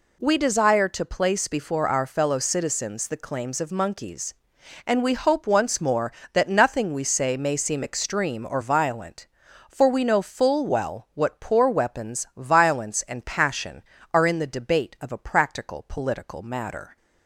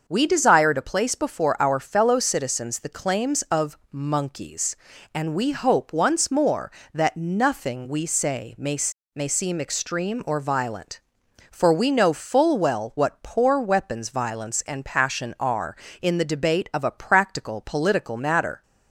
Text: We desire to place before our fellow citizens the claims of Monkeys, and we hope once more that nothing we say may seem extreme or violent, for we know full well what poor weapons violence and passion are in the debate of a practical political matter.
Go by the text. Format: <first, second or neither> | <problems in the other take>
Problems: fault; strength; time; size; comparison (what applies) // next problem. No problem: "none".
first | starts louder than the rest; until 1.0 s; 6.5 dB // pauses between "of" and "Monkeys"; slight; at 3.7 s; 0.16 s long // says "may" twice; at 9.1 s